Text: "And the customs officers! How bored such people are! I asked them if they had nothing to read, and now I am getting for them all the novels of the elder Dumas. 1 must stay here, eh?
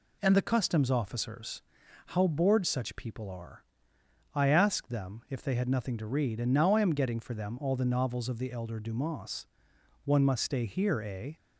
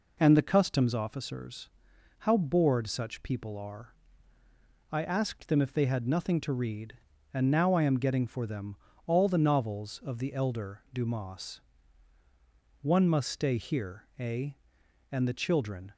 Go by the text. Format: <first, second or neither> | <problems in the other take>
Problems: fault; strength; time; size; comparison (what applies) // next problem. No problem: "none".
first | pauses between "them" and "all"; slight; at 8.7 s; 0.30 s long // goes on to say "And the children"; noticeable; from 15.1 s on; 0.80 s long